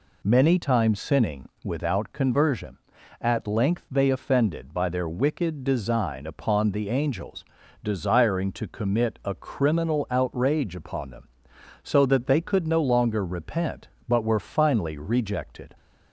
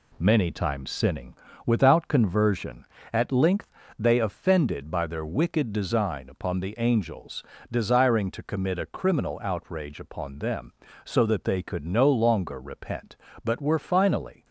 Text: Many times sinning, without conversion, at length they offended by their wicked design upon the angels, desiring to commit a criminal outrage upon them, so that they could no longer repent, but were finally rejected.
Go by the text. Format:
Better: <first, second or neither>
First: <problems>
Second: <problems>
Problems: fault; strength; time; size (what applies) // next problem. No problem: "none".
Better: first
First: none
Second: pauses between "length" and "they"; slight; at 3.7 s; 0.28 s long // stops before "rejected"; at 14.4 s